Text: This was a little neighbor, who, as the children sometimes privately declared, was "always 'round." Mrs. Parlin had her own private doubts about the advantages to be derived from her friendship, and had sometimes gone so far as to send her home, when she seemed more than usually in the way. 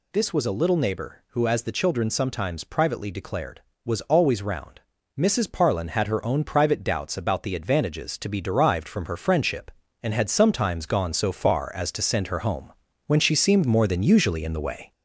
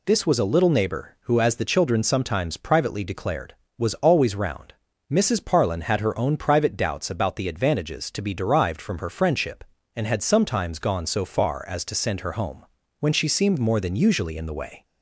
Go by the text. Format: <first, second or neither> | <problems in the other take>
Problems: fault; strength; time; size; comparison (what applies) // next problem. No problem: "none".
second | gets louder; throughout; 3.5 dB